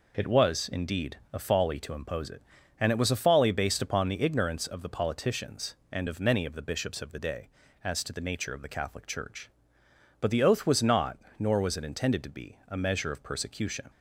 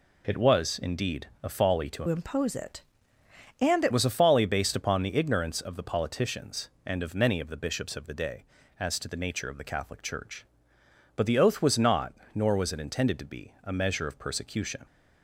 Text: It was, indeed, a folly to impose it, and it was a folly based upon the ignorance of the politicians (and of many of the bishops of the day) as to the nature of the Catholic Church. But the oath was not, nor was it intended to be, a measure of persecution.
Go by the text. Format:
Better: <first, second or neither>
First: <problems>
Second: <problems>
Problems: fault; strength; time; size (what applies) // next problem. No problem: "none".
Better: first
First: none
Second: changes voice from "impose" to "it"; from 2.0 to 3.9 s; 1.9 s long